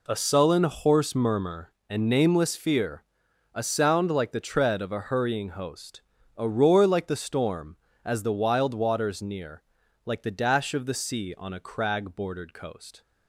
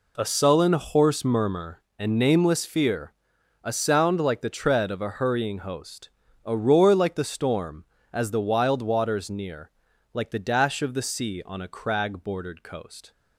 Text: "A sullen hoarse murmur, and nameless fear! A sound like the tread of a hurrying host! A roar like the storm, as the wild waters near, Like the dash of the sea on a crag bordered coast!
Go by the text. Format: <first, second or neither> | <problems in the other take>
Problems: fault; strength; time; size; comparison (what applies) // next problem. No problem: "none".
neither | none